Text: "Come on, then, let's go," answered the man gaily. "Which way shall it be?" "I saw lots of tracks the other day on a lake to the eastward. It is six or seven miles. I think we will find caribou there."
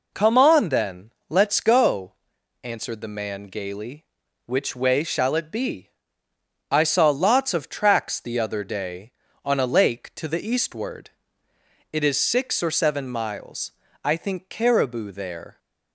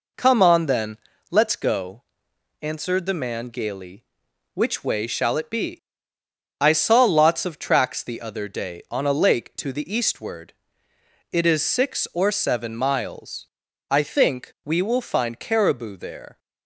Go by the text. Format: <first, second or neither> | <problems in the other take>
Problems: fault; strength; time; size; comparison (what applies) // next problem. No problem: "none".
second | skips "we will find"; at 14.5 s